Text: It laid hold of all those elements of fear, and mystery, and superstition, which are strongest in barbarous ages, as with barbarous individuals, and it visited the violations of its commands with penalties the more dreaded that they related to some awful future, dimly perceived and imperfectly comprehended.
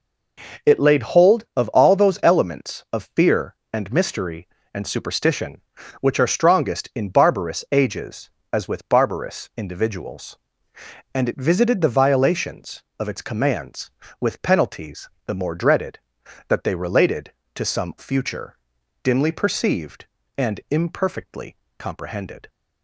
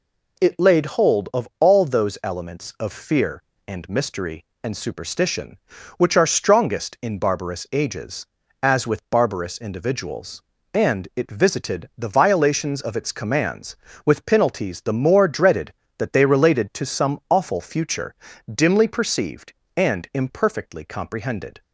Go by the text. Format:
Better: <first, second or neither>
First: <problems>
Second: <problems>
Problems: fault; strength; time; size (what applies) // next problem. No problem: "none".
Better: second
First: pauses between "penalties" and "the"; slight; at 15.0 s; 0.18 s long // skips "awful"; at 17.9 s // pauses between "imperfectly" and "comprehended"; slight; at 21.5 s; 0.22 s long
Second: none